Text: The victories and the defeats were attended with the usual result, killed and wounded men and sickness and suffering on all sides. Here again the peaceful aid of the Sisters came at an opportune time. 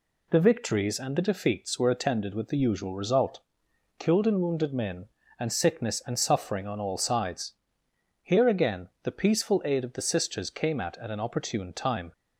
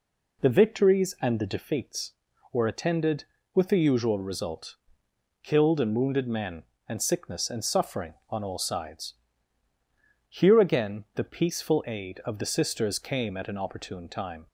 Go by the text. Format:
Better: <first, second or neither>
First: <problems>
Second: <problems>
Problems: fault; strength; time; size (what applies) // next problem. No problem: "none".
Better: second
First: says "at" twice; at 10.9 s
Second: none